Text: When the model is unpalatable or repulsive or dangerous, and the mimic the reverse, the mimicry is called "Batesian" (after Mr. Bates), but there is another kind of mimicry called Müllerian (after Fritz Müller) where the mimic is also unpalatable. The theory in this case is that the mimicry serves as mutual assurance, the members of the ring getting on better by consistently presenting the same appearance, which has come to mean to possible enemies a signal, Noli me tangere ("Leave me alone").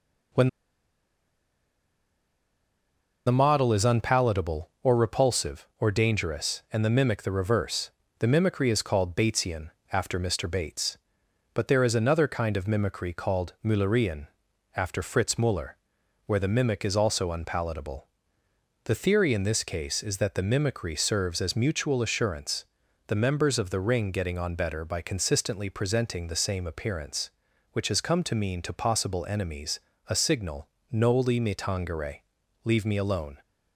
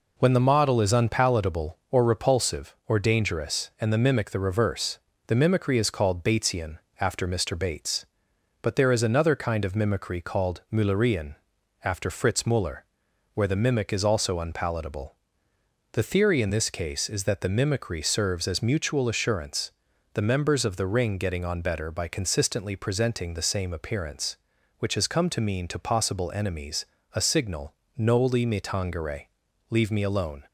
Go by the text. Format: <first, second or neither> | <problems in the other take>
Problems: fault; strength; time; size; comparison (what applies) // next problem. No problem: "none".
second | pauses between "When" and "the"; strong; at 0.4 s; 2.7 s long // pauses between "enemies" and "a"; slight; at 29.7 s; 0.32 s long; slight in the second